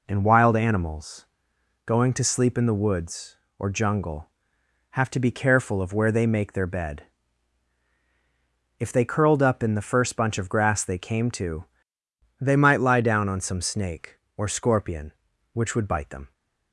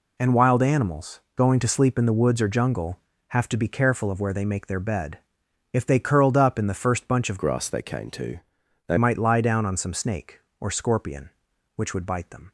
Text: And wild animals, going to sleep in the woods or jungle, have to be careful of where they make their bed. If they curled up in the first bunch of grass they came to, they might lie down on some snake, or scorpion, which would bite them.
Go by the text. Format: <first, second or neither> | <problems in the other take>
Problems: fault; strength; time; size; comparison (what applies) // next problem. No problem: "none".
first | changes voice from "grass" to "they"; from 7.3 to 8.9 s; 1.6 s long